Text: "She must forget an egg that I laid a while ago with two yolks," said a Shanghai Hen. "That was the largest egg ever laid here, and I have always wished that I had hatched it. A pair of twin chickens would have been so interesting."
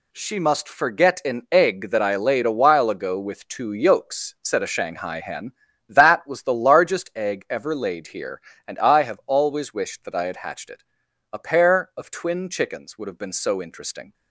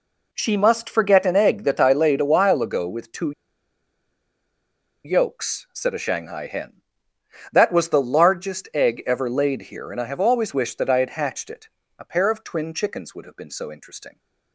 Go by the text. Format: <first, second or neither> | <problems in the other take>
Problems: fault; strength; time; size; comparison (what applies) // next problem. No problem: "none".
first | pauses between "two" and "yolks"; strong; at 3.3 s; 1.7 s long